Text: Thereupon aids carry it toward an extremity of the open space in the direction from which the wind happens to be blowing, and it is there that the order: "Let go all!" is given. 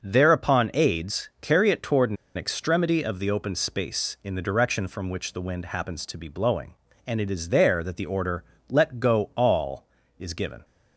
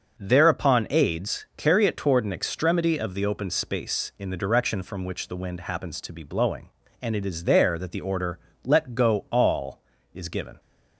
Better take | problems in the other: second | starts louder than the rest; until 1.0 s; 6.5 dB; also in the second // pauses between "an" and "extremity"; slight; at 2.1 s; 0.20 s long

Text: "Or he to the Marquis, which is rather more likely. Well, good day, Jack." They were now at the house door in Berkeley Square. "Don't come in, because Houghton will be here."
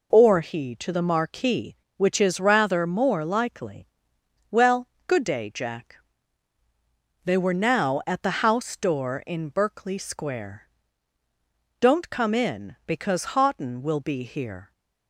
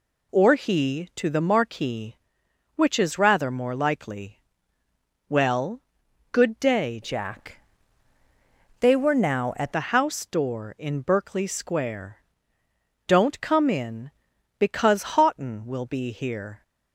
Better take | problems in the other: first | changes voice from "Jack" to "at"; from 7.0 to 9.7 s; 2.7 s long

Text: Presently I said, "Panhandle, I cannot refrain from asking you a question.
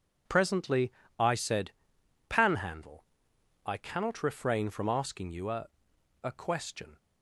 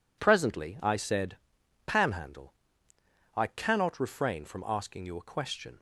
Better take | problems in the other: second | pauses between "Presently" and "I"; slight; at 0.9 s; 0.28 s long // says "a" twice; at 6.2 s

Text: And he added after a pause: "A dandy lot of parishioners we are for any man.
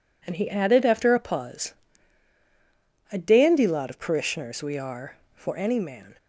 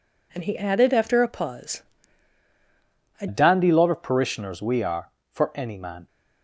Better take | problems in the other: first | changes voice at "dandy"; from 3.2 s on; 2.8 s long

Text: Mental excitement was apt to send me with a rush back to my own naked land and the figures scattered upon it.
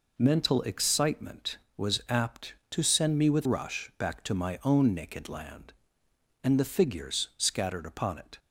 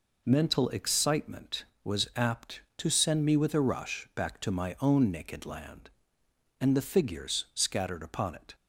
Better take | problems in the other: second | skips "a"; at 3.4 s

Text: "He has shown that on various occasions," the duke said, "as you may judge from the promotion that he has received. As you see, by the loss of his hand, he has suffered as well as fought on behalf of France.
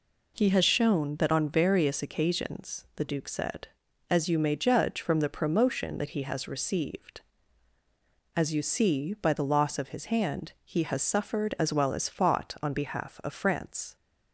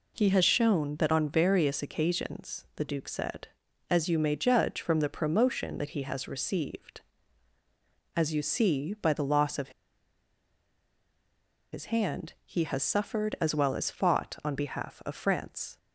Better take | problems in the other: first | pauses between "of" and "his"; strong; at 9.7 s; 2.0 s long

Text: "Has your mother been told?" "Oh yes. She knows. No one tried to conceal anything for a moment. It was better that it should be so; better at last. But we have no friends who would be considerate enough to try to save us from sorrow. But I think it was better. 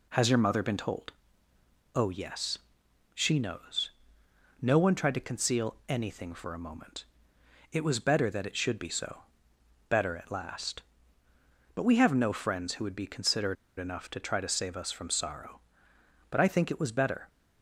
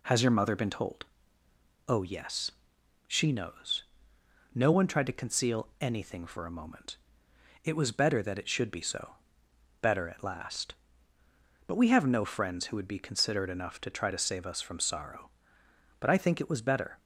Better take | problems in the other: second | pauses between "considerate" and "enough"; slight; at 13.5 s; 0.24 s long

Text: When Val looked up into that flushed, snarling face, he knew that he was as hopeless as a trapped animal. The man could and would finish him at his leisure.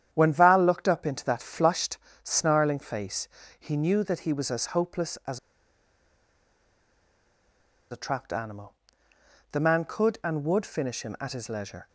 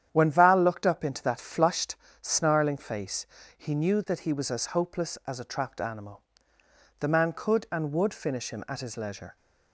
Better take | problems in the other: second | starts louder than the rest; strong; until 1.1 s; 9.5 dB; strong in the second // pauses between "as" and "a"; strong; at 5.3 s; 2.5 s long

